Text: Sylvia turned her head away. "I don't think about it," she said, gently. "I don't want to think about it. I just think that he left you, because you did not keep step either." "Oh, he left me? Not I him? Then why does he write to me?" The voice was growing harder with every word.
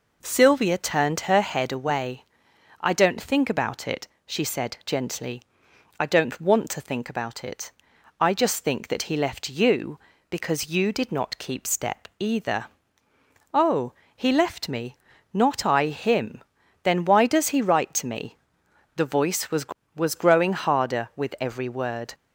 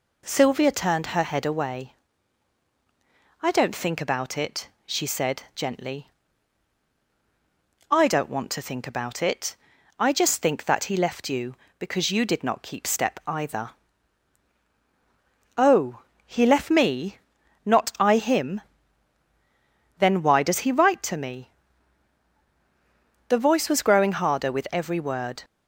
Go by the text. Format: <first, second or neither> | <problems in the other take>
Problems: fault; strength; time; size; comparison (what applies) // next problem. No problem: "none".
second | says "was" twice; at 19.9 s